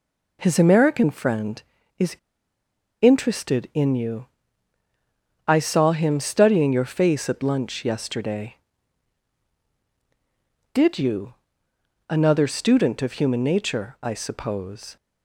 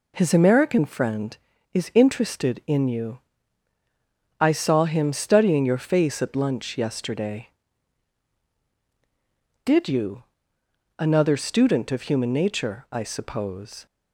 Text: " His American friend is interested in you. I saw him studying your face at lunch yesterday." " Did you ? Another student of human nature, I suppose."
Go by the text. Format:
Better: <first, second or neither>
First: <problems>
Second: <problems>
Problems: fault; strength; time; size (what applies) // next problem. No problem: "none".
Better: second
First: pauses between "is" and "interested"; noticeable; at 2.1 s; 0.85 s long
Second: none